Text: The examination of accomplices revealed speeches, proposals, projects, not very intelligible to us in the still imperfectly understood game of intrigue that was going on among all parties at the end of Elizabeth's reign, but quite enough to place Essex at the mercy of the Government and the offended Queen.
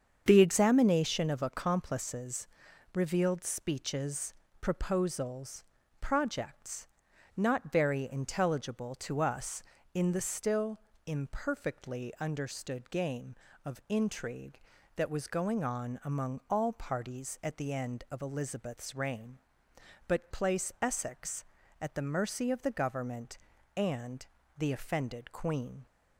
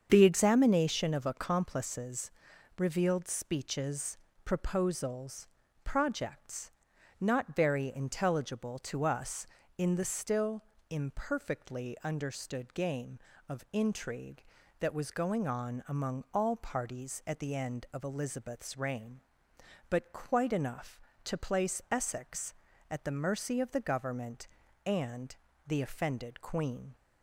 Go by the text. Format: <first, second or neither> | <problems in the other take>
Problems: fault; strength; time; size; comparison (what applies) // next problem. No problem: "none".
second | starts louder than the rest; strong; until 1.2 s; 7.5 dB; strong in the second // pauses between "accomplices" and "revealed"; noticeable; at 2.4 s; 0.46 s long; noticeable in the second // pauses between "still" and "imperfectly"; slight; at 10.7 s; 0.26 s long; slight in the second // skips "quite enough to"; at 20.2 s // pauses between "and" and "the"; slight; at 24.2 s; 0.32 s long; slight in the second